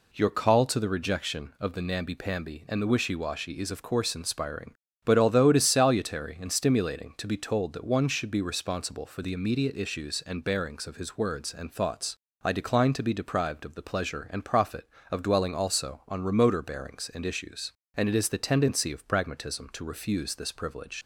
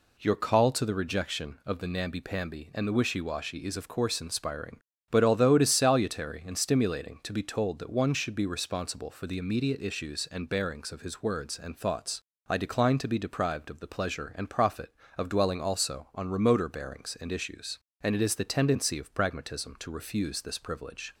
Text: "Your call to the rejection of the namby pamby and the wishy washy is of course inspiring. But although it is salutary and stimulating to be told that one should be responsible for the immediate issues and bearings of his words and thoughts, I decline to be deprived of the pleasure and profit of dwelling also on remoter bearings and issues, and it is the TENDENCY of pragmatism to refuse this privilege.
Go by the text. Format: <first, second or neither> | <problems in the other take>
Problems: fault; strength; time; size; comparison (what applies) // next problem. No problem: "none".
second | leaves "privilege" unfinished; at 21.0 s; 60 ms